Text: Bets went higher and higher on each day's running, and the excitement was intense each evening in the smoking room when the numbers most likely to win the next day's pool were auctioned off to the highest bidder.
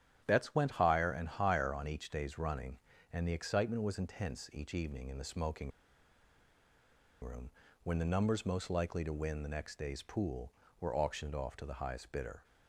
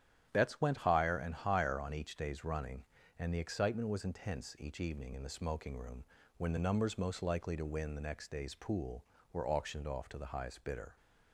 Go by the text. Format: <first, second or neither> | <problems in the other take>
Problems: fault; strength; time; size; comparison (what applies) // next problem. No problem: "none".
second | starts louder than the rest; strong; until 1.2 s; 10.5 dB; strong in the second // pauses between "smoking" and "room"; strong; at 5.7 s; 1.5 s long // pauses between "room" and "when"; slight; at 7.4 s; 0.32 s long; slight in the second